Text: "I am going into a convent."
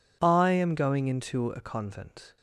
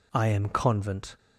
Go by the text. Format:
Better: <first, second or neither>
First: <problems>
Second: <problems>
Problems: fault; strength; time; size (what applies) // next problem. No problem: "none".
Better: first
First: none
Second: skips "going into a"; at 0.4 s